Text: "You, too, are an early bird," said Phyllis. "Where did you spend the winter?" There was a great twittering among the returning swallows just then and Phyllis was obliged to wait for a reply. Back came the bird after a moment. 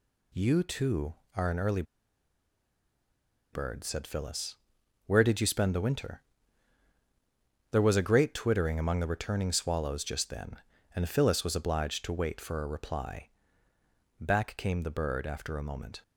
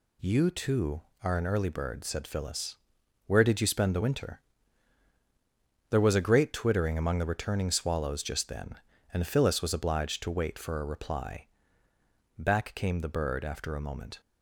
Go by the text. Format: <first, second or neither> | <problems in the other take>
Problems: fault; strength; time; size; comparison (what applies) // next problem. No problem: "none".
second | pauses between "early" and "bird"; strong; at 1.8 s; 1.6 s long